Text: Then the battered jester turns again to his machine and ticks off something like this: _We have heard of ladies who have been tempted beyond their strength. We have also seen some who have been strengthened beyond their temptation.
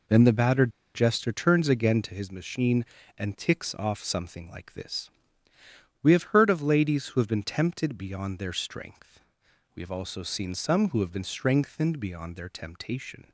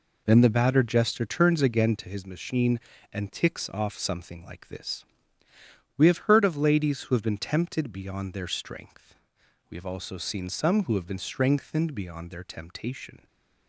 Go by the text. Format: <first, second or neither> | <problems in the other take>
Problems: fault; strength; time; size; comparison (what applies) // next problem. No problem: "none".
second | pauses between "battered" and "jester"; slight; at 0.7 s; 0.24 s long